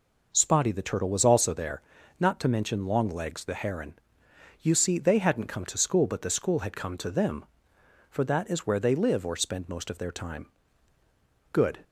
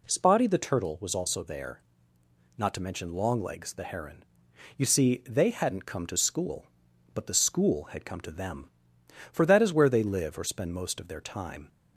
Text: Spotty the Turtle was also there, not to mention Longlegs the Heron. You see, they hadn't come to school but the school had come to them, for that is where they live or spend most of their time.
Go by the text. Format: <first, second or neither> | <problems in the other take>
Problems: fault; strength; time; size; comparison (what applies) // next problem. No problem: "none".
second | goes on to say "Good"; slight; from 11.5 s on; 0.28 s long